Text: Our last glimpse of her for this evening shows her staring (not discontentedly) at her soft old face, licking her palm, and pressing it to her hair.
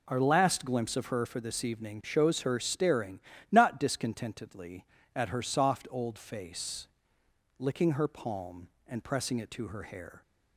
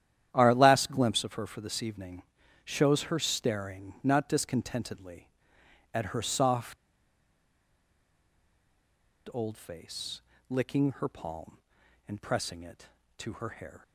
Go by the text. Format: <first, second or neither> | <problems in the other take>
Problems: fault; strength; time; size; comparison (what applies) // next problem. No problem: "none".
first | starts louder than the rest; strong; until 1.3 s; 11 dB // pauses between "evening" and "shows"; at 2.2 s; 0.42 s long // pauses between "soft" and "old"; strong; at 6.7 s; 2.5 s long